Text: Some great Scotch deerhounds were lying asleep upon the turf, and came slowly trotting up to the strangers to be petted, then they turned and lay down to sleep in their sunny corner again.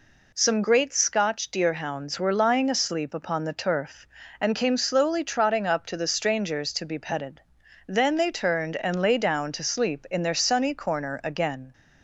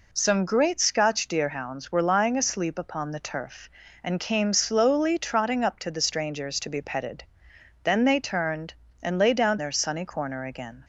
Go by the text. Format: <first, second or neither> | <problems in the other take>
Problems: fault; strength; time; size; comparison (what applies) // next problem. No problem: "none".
first | skips "to sleep in"; at 9.5 s